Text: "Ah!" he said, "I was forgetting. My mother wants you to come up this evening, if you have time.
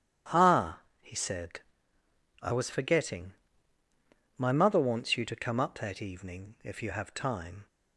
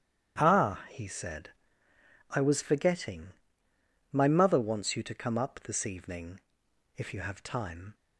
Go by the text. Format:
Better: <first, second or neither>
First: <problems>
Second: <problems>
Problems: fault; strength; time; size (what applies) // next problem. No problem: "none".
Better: second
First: starts louder than the rest; strong; until 1.5 s; 10.5 dB // says "that" for "this"; at 5.7 s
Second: starts louder than the rest; strong; until 1.4 s; 11 dB